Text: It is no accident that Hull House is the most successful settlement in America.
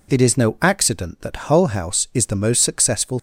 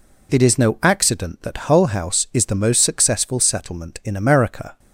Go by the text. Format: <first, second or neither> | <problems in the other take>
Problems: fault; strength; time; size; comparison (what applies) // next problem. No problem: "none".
second | stops before "settlement in America"; at 3.1 s